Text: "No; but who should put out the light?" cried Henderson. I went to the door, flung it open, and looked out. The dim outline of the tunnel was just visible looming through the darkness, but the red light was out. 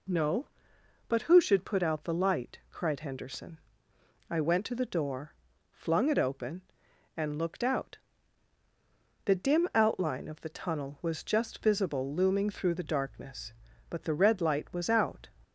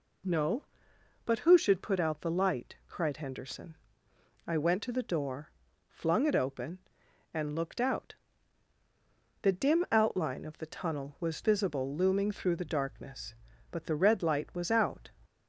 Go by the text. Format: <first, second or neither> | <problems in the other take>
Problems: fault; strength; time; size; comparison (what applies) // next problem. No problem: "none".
first | skips "just"; at 11.4 s